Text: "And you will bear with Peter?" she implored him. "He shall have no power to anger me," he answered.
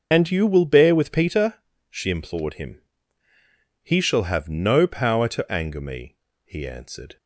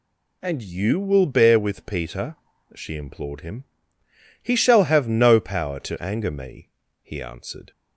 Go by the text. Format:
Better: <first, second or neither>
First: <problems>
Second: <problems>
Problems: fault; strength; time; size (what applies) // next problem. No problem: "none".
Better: second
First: loses the start of "And"; at 0.1 s; 85 ms // starts louder than the rest; until 1.1 s; 6.5 dB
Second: none